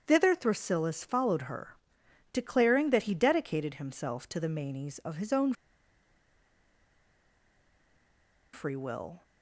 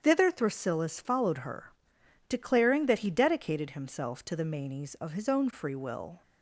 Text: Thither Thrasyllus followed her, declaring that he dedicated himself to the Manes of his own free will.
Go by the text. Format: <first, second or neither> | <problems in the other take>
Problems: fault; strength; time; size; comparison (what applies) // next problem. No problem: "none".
second | starts louder than the rest; strong; until 1.0 s; 8.5 dB; strong in the second // pauses between "own" and "free"; strong; at 5.5 s; 3.0 s long